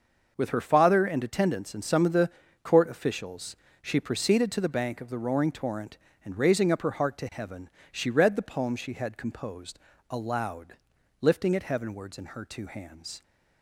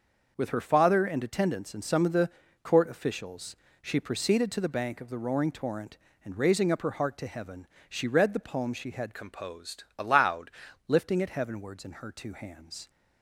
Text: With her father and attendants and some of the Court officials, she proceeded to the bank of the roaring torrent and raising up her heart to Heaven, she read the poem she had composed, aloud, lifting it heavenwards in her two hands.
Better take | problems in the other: first | starts louder than the rest; noticeable; until 1.3 s; 6 dB; noticeable in the first // pauses between "the" and "Court"; slight; at 2.3 s; 0.32 s long; slight in the first // changes voice from "composed" to "aloud"; from 9.1 to 10.5 s; 1.4 s long

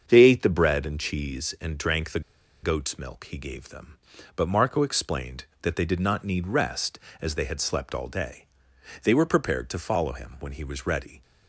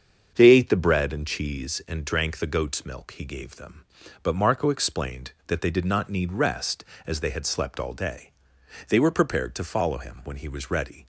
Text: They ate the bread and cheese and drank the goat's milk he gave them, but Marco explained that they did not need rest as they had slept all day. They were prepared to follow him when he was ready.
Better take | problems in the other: second | starts louder than the rest; strong; until 1.0 s; 7 dB; strong in the second // pauses between "the" and "goat's"; at 2.2 s; 0.42 s long

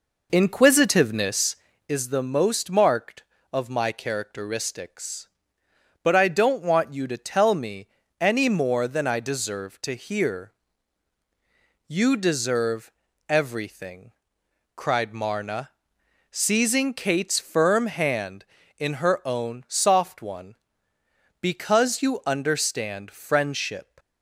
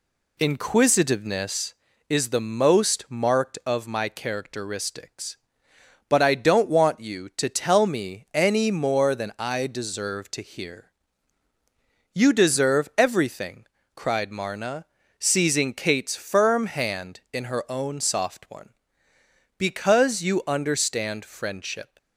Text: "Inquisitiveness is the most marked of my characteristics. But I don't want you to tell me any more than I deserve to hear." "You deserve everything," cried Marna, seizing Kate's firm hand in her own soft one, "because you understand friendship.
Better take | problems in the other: second | starts louder than the rest; noticeable; until 2.0 s; 4.5 dB // pauses between "me" and "any"; slight; at 7.8 s; 0.32 s long // pauses between "deserve" and "everything"; slight; at 12.9 s; 0.36 s long

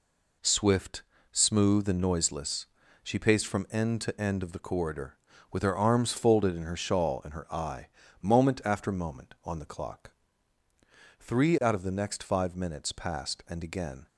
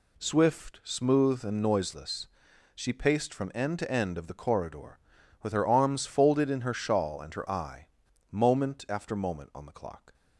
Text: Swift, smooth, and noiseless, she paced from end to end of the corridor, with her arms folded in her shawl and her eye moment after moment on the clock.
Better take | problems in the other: second | pauses between "eye" and "moment"; slight; at 7.8 s; 0.34 s long; also in the second // goes on to say "Three out of the next five minutes passed and again"; strong; from 11.1 s on; 2.8 s long

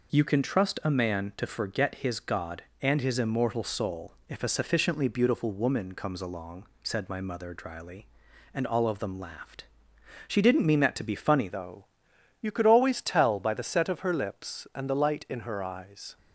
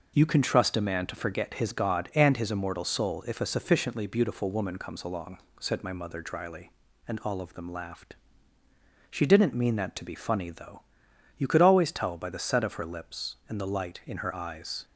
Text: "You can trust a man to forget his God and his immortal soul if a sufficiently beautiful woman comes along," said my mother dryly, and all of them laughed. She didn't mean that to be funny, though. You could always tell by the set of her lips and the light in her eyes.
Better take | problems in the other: second | changes voice at "though"; from 11.4 s on; 4.7 s long

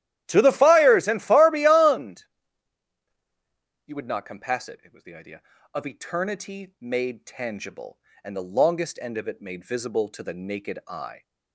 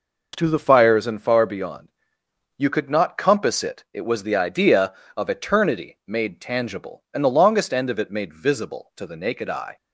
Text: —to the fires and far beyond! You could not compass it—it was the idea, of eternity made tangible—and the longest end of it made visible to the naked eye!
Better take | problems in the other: second | starts louder than the rest; strong; until 1.2 s; 12.5 dB // says "would" for "could"; at 3.9 s

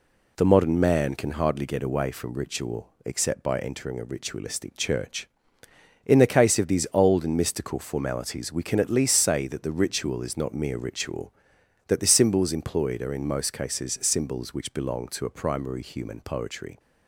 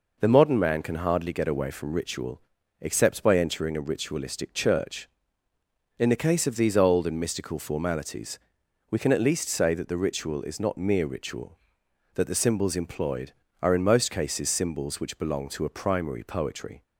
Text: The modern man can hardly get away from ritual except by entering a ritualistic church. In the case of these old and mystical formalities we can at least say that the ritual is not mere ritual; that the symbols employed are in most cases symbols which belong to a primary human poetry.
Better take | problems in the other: first | pauses between "ritual" and "except"; at 2.3 s; 0.42 s long; slight in the first // pauses between "formalities" and "we"; noticeable; at 8.3 s; 0.52 s long // skips "human"; at 16.2 s

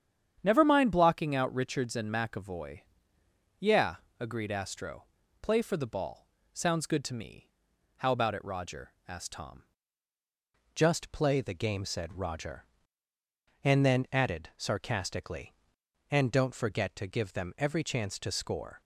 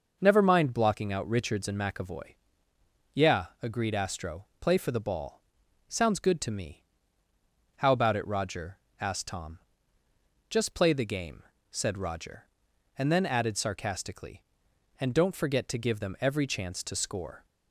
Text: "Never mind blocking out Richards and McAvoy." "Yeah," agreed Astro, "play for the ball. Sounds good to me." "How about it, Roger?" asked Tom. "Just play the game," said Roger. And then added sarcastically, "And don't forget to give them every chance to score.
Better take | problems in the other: second | starts louder than the rest; strong; until 1.4 s; 8.5 dB // changes voice at "Just"; from 10.7 s on; 8.1 s long

